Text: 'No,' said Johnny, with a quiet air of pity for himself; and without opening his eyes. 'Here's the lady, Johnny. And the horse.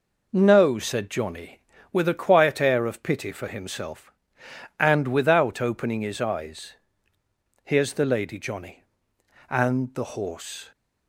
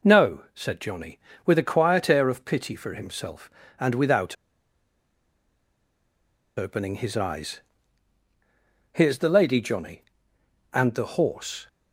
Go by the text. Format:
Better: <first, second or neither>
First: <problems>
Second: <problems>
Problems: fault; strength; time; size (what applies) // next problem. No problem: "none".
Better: first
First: none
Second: pauses between "without" and "opening"; strong; at 4.3 s; 2.2 s long